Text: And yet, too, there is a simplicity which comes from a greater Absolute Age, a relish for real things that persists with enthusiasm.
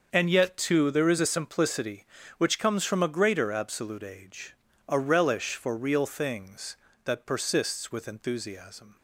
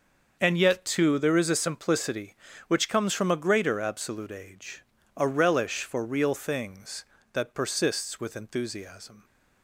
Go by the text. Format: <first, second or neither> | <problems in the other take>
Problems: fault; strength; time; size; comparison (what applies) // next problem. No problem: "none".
neither | starts louder than the rest; the same in both